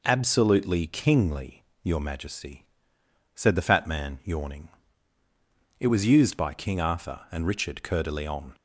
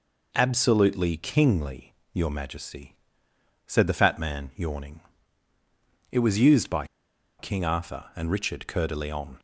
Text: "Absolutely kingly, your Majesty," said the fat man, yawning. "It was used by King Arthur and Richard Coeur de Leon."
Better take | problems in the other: first | pauses between "by" and "King"; noticeable; at 6.8 s; 0.53 s long

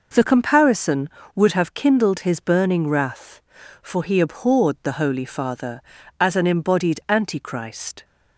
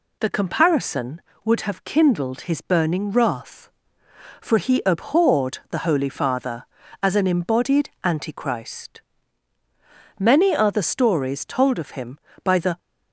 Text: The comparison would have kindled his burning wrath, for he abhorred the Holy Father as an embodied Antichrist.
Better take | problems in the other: first | goes on to say "Many are the stories told of him by the"; strong; from 10.1 s on; 2.6 s long

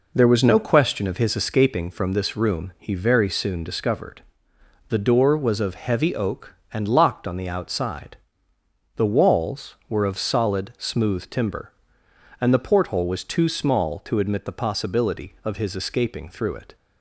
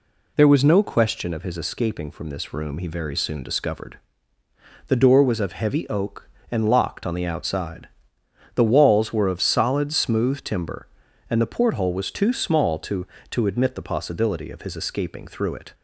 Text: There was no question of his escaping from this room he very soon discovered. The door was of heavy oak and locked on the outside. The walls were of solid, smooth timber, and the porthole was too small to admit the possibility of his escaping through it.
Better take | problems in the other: first | says "to" twice; at 13.3 s

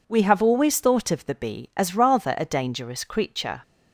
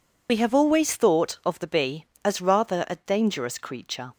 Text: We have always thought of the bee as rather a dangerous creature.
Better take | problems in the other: first | loses the start of "We"; at 0.2 s; 60 ms

